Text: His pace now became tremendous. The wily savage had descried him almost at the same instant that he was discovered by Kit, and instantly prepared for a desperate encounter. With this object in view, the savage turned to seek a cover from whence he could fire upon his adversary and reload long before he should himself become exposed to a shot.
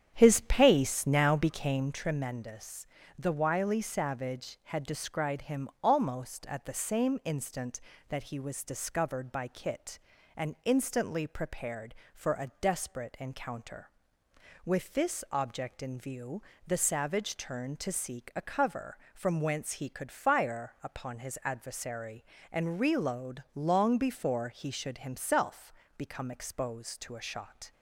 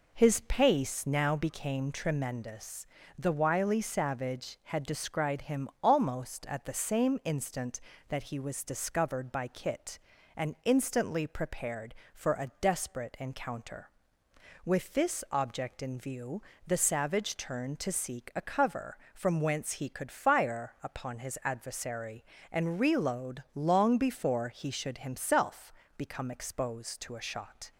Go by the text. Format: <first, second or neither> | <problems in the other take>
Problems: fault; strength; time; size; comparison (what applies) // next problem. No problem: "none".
second | starts louder than the rest; strong; until 2.0 s; 9 dB // pauses between "himself" and "become"; slight; at 25.7 s; 0.24 s long; slight in the second